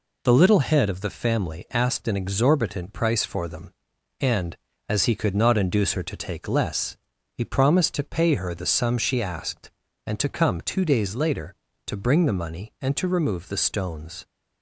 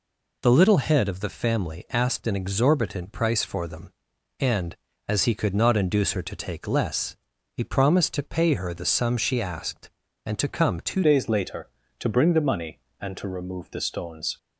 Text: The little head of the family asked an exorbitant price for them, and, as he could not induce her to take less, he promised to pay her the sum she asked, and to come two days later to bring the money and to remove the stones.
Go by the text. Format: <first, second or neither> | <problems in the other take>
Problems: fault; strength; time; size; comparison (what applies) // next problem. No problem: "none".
first | changes voice at "days"; from 11.0 s on; 3.3 s long